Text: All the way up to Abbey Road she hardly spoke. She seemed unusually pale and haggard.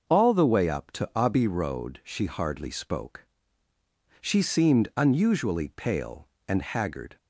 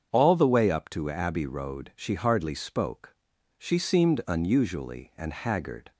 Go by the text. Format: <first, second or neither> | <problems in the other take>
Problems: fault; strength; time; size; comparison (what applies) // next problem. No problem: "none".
first | starts louder than the rest; strong; until 1.1 s; 7.5 dB // skips "pale"; at 5.1 s